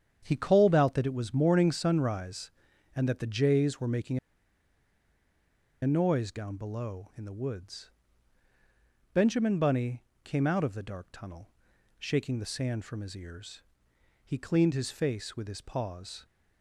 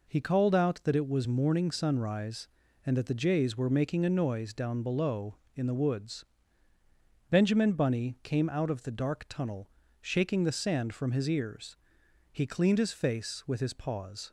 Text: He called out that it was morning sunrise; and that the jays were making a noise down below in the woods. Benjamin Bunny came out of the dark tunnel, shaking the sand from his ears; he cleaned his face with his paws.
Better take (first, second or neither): second